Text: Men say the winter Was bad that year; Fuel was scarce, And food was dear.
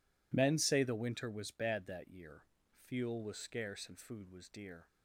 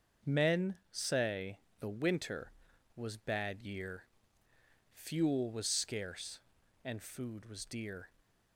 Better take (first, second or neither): first